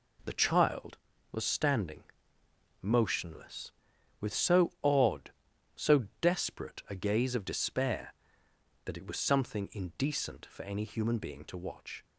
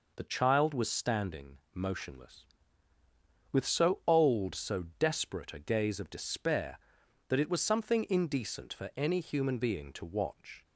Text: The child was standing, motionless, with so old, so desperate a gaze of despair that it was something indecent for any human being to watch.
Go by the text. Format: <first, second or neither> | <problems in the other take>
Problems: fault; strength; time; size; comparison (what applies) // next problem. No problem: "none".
second | says "odd" for "old"; at 4.8 s // pauses between "so" and "desperate"; slight; at 6.0 s; 0.16 s long; slight in the second